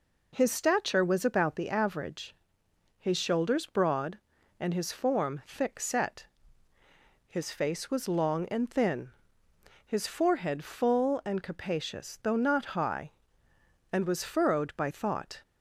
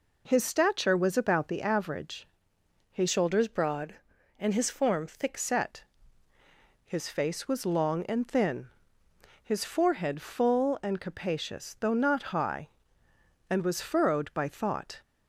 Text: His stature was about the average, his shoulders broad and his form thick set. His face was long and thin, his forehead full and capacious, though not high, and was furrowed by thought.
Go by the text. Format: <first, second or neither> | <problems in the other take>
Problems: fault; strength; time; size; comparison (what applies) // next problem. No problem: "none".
first | changes voice from "shoulders" to "thick"; from 3.0 to 5.3 s; 2.3 s long